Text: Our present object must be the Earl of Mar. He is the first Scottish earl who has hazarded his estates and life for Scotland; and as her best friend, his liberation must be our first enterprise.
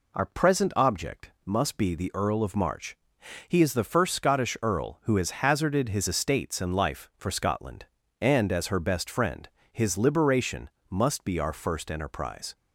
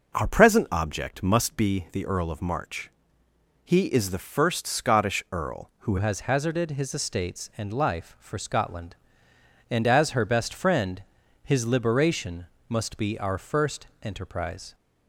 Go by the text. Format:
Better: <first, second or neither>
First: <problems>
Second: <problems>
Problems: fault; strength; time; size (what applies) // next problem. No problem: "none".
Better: first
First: pauses between "liberation" and "must"; slight; at 10.6 s; 0.22 s long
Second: changes voice at "has"; from 5.9 s on; 8.8 s long // pauses between "liberation" and "must"; slight; at 12.4 s; 0.22 s long // pauses between "first" and "enterprise"; slight; at 13.8 s; 0.16 s long